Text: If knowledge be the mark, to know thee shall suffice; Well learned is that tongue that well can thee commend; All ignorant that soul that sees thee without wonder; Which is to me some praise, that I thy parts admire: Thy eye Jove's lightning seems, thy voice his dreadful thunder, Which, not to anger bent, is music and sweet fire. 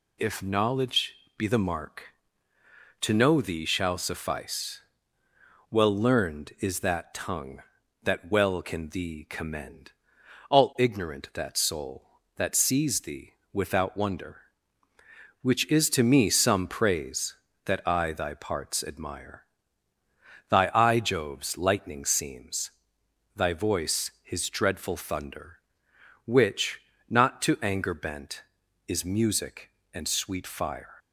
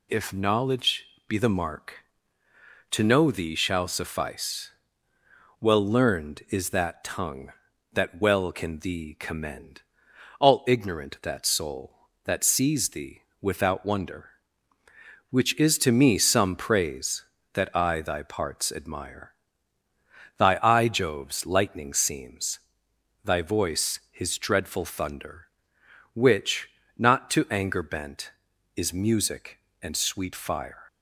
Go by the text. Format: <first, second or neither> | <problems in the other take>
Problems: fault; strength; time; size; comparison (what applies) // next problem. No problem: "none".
neither | pauses between "knowledge" and "be"; slight; the same in both // pauses between "thee" and "without"; slight; the same in both